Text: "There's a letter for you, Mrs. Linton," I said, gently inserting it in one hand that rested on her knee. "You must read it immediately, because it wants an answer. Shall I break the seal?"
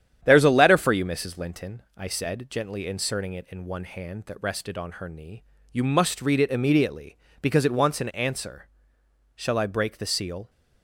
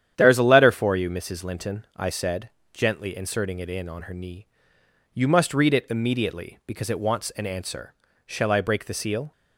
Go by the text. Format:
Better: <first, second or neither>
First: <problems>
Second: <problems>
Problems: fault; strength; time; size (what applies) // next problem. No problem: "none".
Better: first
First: starts louder than the rest; strong; until 1.2 s; 9.5 dB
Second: starts louder than the rest; strong; until 1.1 s; 9.5 dB // skips "one hand that rested"; at 3.8 s